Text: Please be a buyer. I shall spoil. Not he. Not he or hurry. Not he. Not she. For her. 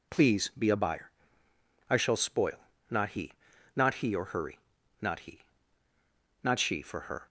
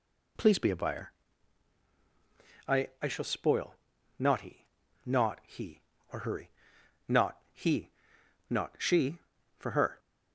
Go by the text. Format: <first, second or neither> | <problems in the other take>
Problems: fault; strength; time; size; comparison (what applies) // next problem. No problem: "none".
first | says "I" twice; at 3.0 s // pauses between "Not" and "he"; slight; at 7.3 s; 0.16 s long